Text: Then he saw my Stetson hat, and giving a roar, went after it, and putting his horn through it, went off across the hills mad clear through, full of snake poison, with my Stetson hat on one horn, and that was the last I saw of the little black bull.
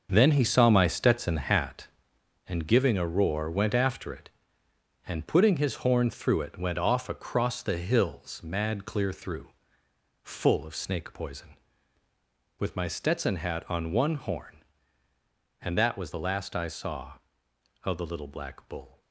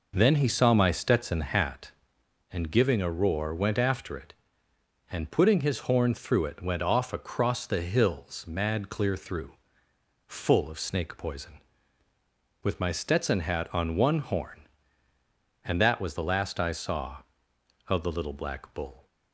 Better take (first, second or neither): second